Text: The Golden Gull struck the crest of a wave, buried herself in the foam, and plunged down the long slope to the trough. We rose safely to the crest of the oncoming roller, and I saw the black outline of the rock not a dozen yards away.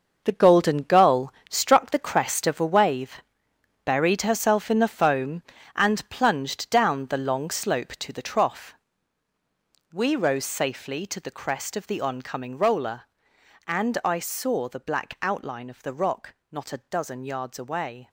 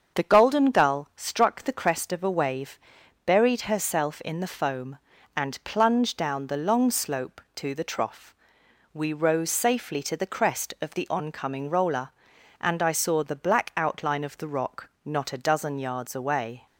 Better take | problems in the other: second | gets quieter; strong; throughout; 10 dB // starts louder than the rest; noticeable; until 1.2 s; 6 dB; also in the second // pauses between "Gull" and "struck"; slight; at 1.3 s; 0.16 s long // pauses between "rock" and "not"; slight; at 16.3 s; 0.18 s long; slight in the second

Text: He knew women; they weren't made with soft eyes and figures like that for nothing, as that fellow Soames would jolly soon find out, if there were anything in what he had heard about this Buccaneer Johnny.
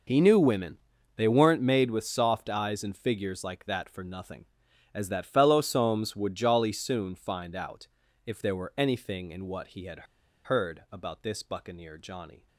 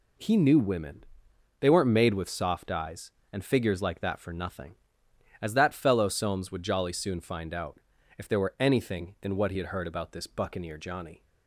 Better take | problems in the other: second | pauses between "had" and "heard"; at 10.0 s; 0.41 s long

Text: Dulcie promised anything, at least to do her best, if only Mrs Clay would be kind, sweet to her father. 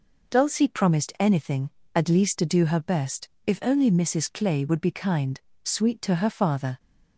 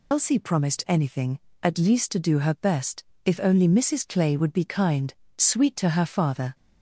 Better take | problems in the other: first | loses the start of "Dulcie"; at 0.1 s; 100 ms

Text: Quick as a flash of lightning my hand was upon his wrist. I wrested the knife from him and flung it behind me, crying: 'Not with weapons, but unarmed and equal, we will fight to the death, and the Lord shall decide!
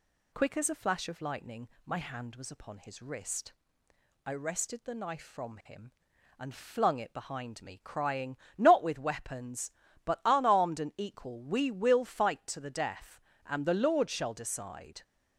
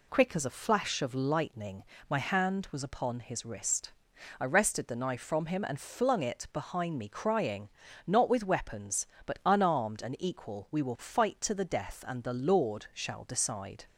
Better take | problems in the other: neither | pauses between "lightning" and "my"; slight; the same in both

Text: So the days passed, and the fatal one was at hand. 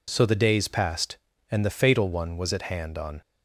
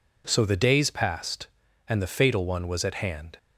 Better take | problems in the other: second | goes on to say "On"; slight; from 2.9 s on; 0.24 s long

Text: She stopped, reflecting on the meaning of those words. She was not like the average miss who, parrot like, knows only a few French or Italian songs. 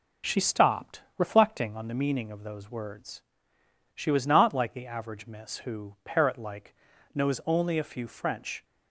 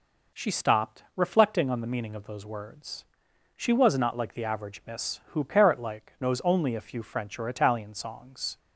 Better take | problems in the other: second | stops before "or Italian songs"; at 8.6 s

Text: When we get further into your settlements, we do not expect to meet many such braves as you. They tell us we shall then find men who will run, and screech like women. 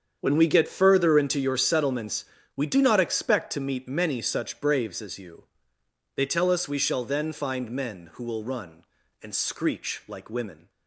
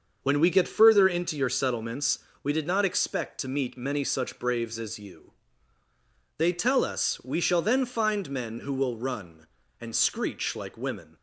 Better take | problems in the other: first | starts louder than the rest; until 1.2 s; 6.5 dB; strong in the first // says "did" for "do"; at 2.5 s

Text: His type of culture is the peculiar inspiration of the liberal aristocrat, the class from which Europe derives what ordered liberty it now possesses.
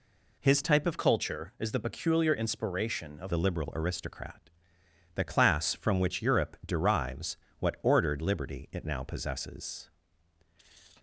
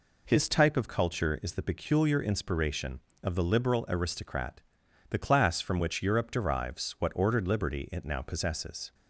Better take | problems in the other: second | changes voice from "culture" to "of"; from 0.9 to 3.3 s; 2.4 s long // pauses between "derives" and "what"; slight; at 7.3 s; 0.22 s long

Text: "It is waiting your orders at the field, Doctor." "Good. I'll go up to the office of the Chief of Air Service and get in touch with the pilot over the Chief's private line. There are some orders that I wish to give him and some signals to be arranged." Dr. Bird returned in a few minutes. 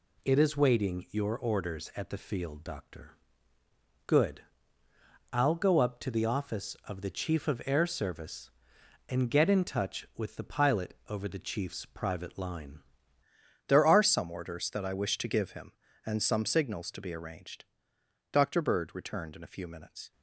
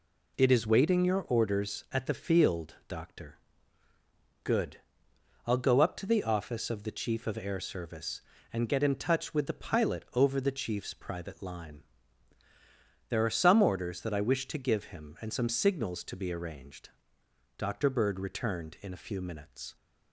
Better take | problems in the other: second | changes voice at "There"; from 13.6 s on; 6.5 s long

